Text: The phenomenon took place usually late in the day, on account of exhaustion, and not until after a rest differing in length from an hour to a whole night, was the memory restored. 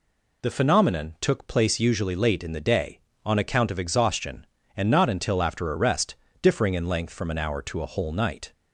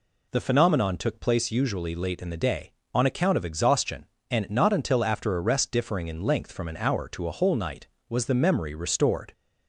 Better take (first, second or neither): second